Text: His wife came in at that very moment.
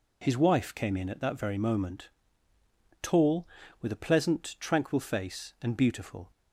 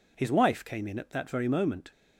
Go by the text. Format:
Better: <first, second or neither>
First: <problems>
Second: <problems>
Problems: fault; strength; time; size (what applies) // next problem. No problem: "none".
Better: second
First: goes on to say "Tall with a pleasant tranquil face and beautiful"; strong; from 3.0 s on; 3.2 s long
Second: none